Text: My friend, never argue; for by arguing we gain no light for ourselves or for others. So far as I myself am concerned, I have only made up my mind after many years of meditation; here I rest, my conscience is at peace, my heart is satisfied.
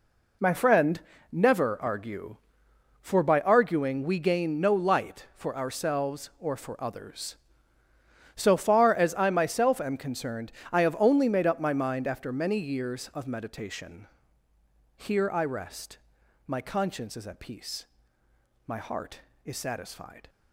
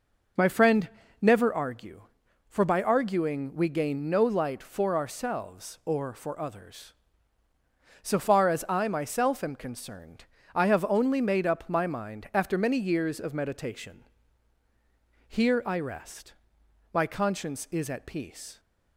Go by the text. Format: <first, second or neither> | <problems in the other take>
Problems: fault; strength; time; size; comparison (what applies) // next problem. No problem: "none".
first | stops before "my heart is satisfied"; at 18.5 s